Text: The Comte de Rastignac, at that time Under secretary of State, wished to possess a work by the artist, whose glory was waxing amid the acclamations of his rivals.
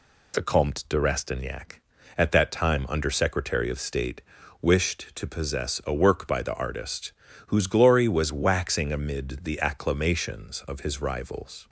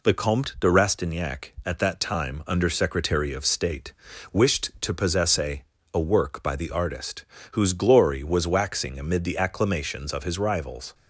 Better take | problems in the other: first | says "a" twice; at 5.9 s

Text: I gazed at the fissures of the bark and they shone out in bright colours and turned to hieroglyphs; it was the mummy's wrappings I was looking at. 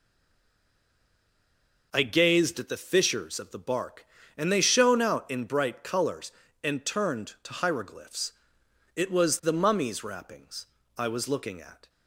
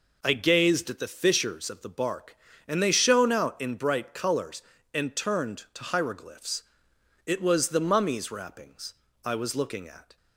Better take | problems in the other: second | stays silent before the first word; noticeable; until 1.9 s; 1.9 s long // pauses between "wrappings" and "I"; slight; at 10.6 s; 0.30 s long; slight in the second

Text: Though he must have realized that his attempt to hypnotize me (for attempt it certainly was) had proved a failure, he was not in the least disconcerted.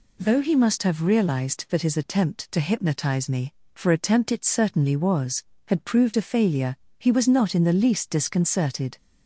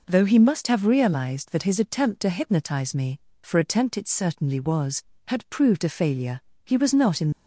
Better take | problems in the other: first | stops before "the least disconcerted"; at 7.3 s

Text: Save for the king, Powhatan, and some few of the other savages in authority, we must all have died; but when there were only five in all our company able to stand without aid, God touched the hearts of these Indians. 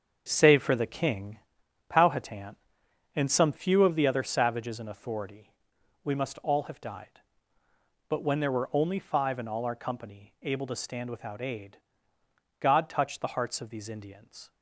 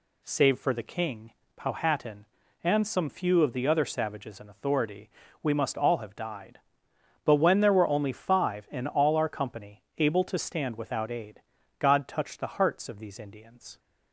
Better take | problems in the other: second | gets quieter; strong; throughout; 9 dB

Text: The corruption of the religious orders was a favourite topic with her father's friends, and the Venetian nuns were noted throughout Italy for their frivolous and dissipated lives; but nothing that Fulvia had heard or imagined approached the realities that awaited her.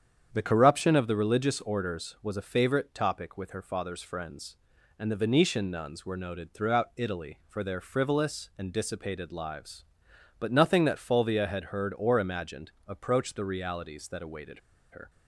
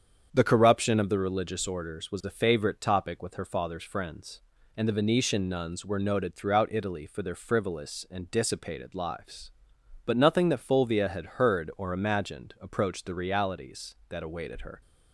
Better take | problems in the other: second | starts louder than the rest; strong; until 1.3 s; 8.5 dB; strong in the second // pauses between "imagined" and "approached"; slight; at 12.7 s; 0.16 s long // pauses between "awaited" and "her"; slight; at 14.5 s; 0.32 s long

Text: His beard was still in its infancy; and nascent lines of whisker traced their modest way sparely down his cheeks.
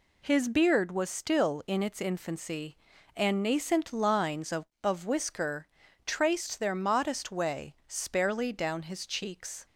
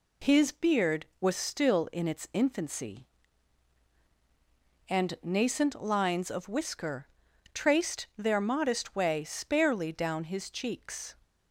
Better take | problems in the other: second | says "of" twice; at 4.8 s // pauses between "whisker" and "traced"; at 5.6 s; 0.38 s long; also in the second

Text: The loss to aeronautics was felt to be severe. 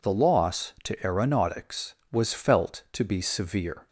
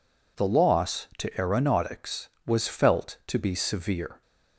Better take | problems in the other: neither | none

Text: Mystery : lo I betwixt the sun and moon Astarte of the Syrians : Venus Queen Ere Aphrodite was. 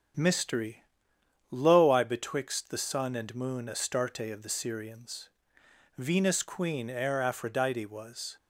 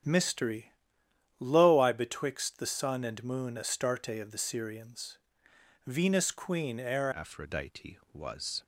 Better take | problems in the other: first | starts louder than the rest; strong; until 1.7 s; 9 dB; strong in the first // changes voice at "Aphrodite"; from 7.1 s on; 1.5 s long

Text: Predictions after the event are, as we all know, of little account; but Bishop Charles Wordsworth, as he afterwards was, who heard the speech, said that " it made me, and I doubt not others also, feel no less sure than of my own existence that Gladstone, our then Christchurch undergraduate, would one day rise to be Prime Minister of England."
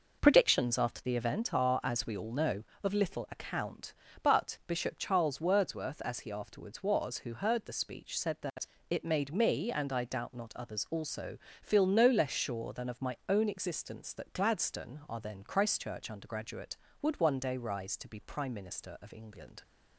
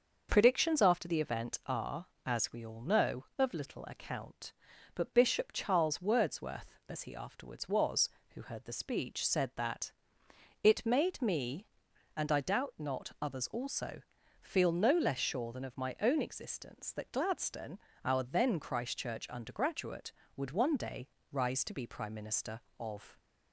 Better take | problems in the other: first | starts louder than the rest; noticeable; until 1.3 s; 6 dB // pauses between "day" and "rise"; slight; at 21.0 s; 0.24 s long // stops before "England"; at 23.1 s

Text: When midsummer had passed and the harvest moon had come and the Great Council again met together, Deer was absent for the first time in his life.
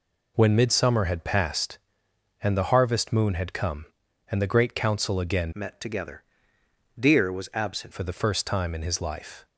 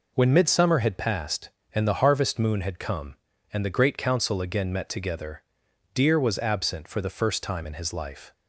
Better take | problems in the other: second | changes voice from "met" to "absent"; from 5.5 to 7.9 s; 2.4 s long

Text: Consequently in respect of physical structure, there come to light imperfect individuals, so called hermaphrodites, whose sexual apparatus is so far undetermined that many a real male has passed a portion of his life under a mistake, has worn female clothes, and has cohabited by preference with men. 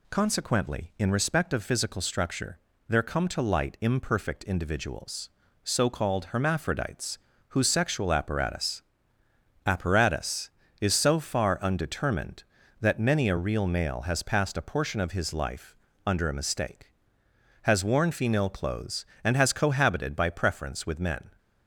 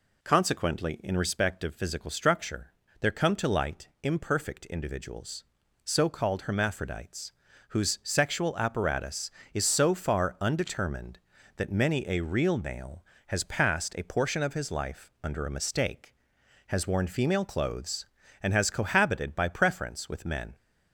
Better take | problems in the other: second | says "apparatus" twice; at 9.6 s // pauses between "life" and "under"; slight; at 15.7 s; 0.32 s long

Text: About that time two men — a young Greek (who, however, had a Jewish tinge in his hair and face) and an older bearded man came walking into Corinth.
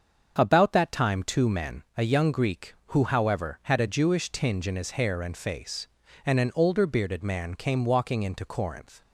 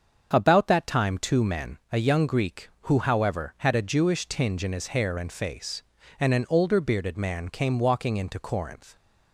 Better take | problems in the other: neither | starts louder than the rest; the same in both

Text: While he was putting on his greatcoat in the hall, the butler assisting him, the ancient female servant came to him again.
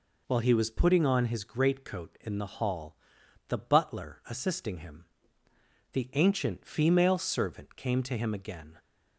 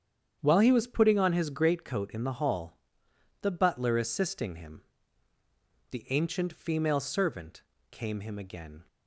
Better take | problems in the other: first | starts louder than the rest; strong; until 1.4 s; 8.5 dB // pauses between "servant" and "came"; slight; at 7.6 s; 0.28 s long // skips "to"; at 8.2 s

